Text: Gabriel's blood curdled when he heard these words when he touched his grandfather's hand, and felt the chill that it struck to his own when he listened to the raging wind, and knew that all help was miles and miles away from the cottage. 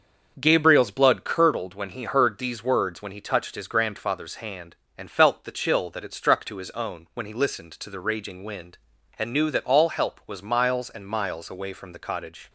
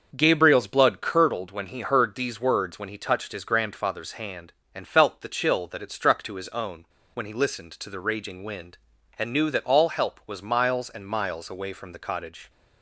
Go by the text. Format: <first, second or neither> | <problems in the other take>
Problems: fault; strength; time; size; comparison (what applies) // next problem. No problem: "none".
first | starts louder than the rest; until 1.1 s; 6.5 dB; also in the first // pauses between "own" and "when"; slight; at 6.8 s; 0.30 s long